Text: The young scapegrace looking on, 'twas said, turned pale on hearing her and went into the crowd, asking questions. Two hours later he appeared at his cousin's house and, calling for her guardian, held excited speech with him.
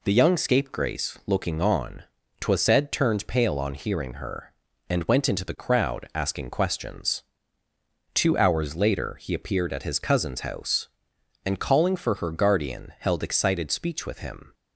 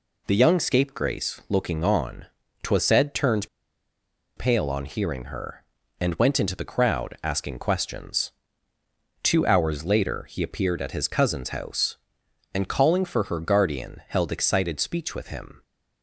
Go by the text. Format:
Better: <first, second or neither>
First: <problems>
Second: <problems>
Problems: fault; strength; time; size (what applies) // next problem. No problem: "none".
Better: first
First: none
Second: pauses between "turned" and "pale"; noticeable; at 3.4 s; 0.90 s long